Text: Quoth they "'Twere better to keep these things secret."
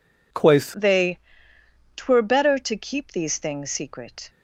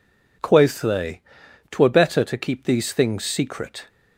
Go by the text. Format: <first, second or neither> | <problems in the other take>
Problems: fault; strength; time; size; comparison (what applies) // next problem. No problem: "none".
second | changes voice at "they"; from 0.7 s on; 3.5 s long // pauses between "they" and "Twere"; noticeable; at 1.1 s; 0.78 s long; noticeable in the second